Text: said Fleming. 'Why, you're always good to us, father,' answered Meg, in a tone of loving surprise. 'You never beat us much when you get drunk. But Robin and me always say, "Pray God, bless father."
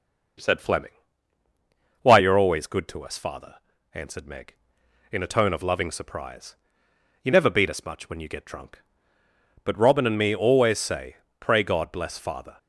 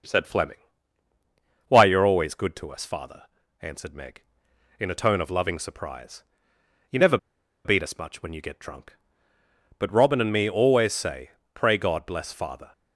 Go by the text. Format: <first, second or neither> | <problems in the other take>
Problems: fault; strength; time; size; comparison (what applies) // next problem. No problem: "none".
first | starts louder than the rest; noticeable; until 2.1 s; 6 dB; noticeable in the first // pauses between "never" and "beat"; noticeable; at 7.1 s; 0.48 s long